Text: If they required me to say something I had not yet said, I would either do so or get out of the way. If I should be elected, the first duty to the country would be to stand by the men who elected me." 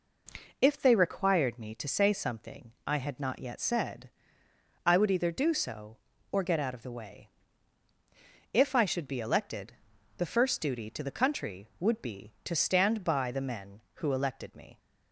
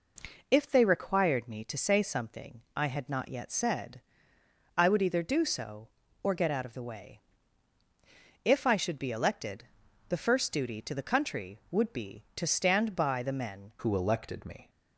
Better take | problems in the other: first | changes voice at "who"; from 13.7 s on; 0.9 s long

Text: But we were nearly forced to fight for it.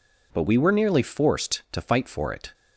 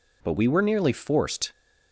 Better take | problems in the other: first | stops before "to fight for it"; at 1.5 s

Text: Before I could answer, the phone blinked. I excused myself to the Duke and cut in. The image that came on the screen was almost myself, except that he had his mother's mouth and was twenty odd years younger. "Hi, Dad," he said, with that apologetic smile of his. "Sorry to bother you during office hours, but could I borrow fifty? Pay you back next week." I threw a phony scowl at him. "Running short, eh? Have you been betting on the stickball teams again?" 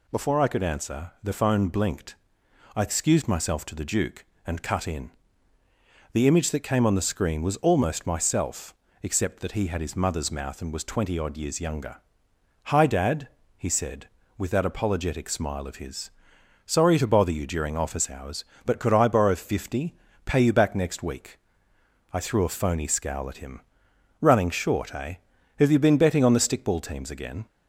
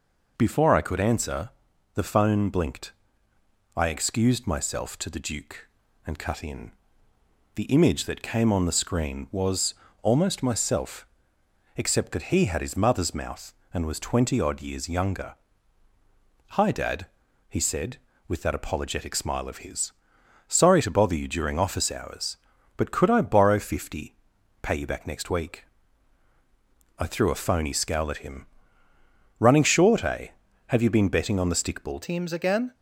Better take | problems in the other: first | pauses between "was" and "almost"; slight; at 9.7 s; 0.26 s long // changes voice at "teams"; from 32.0 s on; 0.7 s long

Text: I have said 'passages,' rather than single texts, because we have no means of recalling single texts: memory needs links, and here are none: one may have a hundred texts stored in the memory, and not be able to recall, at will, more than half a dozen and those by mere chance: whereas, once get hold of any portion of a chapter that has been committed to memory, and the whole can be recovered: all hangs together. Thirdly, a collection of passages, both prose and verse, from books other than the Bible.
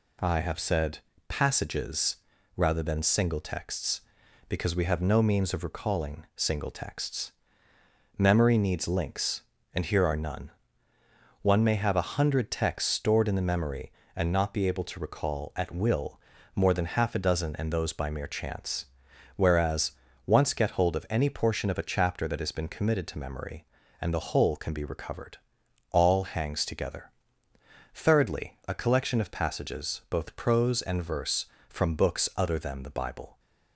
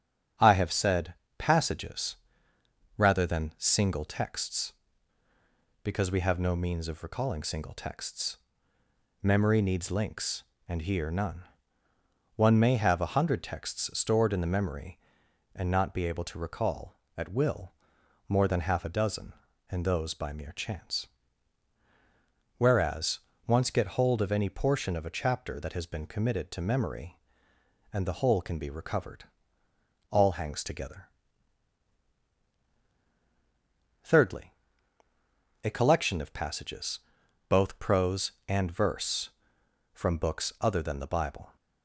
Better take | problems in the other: first | starts louder than the rest; strong; until 1.6 s; 9 dB // pauses between "said" and "passages"; slight; at 1.1 s; 0.24 s long; slight in the first // skips "are"; at 11.0 s

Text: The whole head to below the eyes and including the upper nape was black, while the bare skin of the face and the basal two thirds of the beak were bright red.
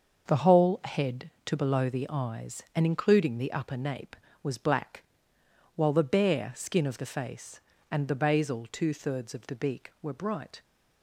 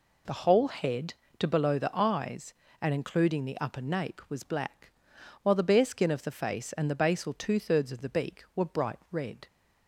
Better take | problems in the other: second | starts louder than the rest; until 1.2 s; 6.5 dB // stops before "red"; at 10.6 s

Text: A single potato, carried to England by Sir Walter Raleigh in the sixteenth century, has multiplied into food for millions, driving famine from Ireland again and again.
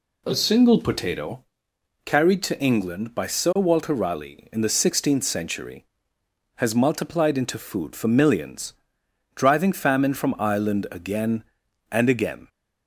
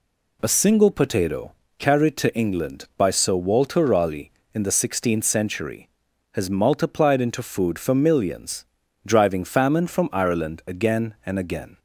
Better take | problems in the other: neither | none

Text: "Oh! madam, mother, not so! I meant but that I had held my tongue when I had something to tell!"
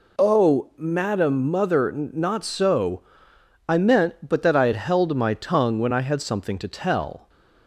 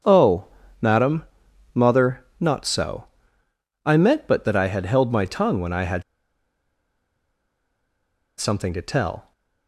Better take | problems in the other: first | starts louder than the rest; strong; until 1.8 s; 7 dB // pauses between "had" and "something"; strong; at 6.0 s; 2.3 s long

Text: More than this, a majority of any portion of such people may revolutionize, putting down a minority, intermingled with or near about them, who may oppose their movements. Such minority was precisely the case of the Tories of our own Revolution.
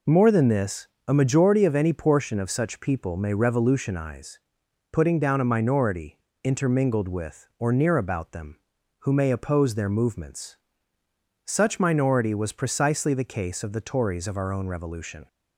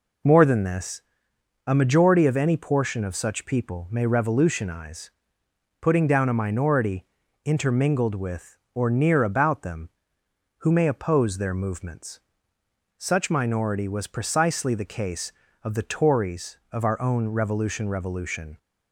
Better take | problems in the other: first | says "Revolution" twice; at 17.8 s

